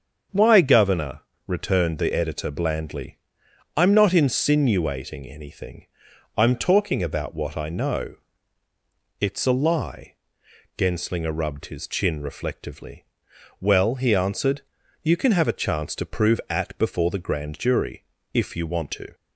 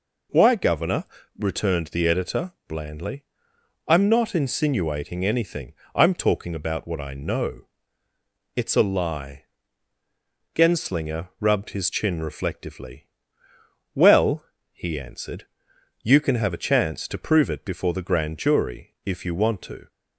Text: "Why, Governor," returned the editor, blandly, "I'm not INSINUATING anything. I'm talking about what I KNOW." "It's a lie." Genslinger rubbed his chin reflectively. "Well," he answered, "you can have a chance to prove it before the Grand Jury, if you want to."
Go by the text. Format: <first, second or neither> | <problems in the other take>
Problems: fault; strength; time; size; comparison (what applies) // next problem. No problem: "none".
second | starts louder than the rest; until 1.5 s; 7 dB // says "at" for "it"; at 16.5 s